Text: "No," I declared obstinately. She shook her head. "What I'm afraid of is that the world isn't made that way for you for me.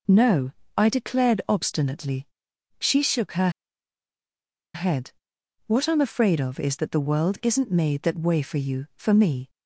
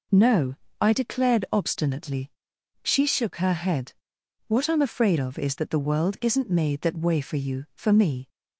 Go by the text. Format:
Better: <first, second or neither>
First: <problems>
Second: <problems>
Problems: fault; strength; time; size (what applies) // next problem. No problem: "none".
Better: second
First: pauses between "her" and "head"; strong; at 3.4 s; 1.2 s long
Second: none